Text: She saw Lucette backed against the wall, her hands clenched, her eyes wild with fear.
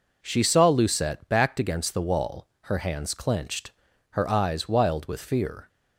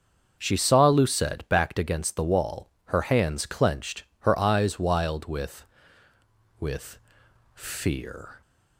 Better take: first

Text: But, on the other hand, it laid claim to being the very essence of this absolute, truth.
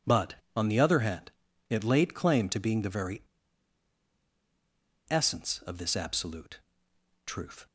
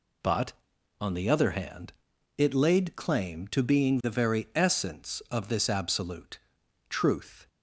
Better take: second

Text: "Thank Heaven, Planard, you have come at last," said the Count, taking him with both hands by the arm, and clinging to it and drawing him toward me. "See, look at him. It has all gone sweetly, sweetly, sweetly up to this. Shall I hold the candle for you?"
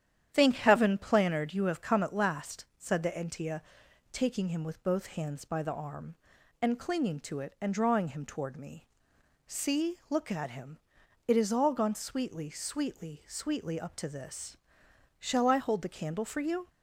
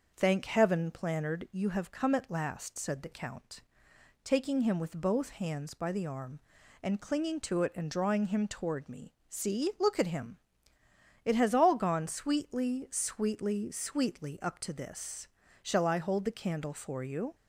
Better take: second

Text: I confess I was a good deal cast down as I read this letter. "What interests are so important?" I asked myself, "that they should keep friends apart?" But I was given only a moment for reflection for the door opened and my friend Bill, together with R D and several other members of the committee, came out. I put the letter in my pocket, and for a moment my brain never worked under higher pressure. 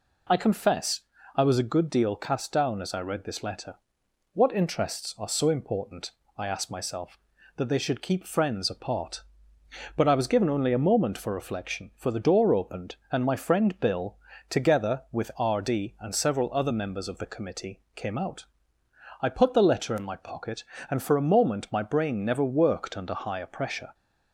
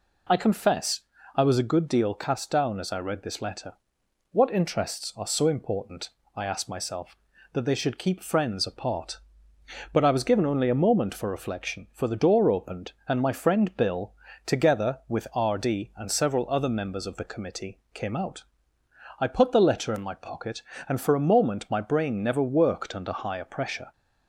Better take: neither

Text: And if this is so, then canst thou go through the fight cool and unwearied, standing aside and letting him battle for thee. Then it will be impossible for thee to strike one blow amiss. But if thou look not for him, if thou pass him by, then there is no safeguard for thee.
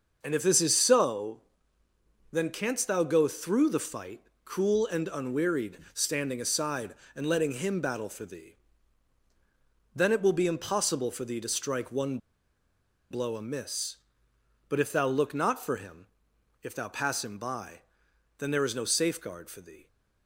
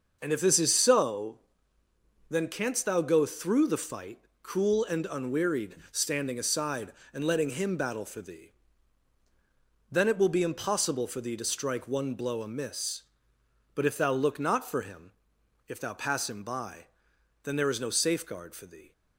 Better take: second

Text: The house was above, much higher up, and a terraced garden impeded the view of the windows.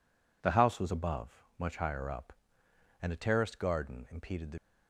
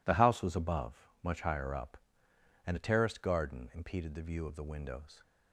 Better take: second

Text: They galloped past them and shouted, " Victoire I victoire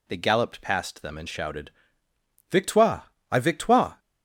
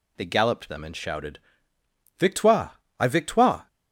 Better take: first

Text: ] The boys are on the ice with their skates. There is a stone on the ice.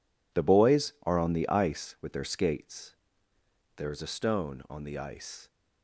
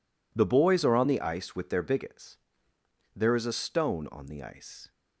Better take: first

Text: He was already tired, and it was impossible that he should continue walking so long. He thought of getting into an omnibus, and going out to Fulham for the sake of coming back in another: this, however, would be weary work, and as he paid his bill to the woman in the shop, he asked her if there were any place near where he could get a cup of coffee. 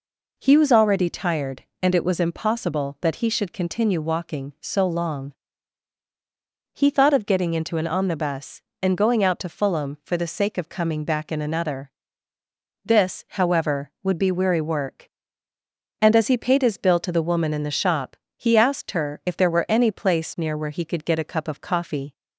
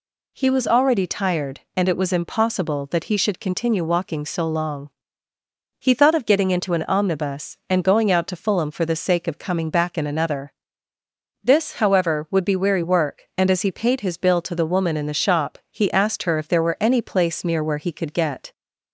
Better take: first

